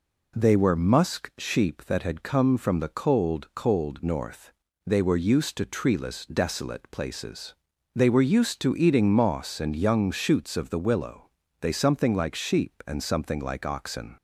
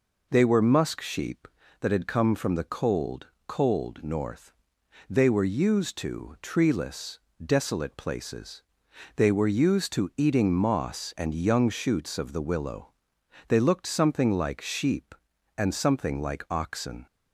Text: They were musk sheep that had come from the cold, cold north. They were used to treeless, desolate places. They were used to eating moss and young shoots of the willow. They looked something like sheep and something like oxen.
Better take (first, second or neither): second